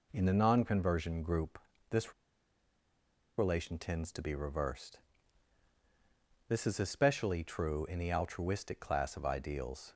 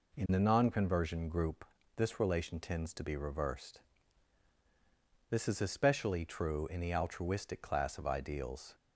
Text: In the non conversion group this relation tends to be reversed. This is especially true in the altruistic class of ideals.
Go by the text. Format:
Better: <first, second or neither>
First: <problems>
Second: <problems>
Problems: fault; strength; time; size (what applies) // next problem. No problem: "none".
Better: second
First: pauses between "group" and "this"; slight; at 1.5 s; 0.32 s long // pauses between "this" and "relation"; strong; at 2.1 s; 1.2 s long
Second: pauses between "group" and "this"; slight; at 1.6 s; 0.32 s long